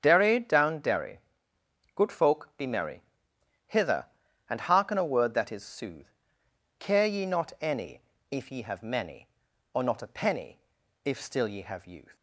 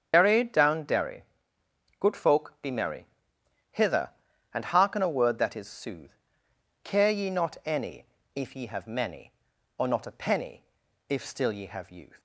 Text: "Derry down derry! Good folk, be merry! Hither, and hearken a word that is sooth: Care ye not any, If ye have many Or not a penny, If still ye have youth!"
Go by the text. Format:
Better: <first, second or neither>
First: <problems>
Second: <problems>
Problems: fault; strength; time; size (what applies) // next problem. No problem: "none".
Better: first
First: starts louder than the rest; strong; until 1.0 s; 8 dB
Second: loses the start of "Derry"; at 0.1 s; 60 ms // starts louder than the rest; strong; until 1.1 s; 7.5 dB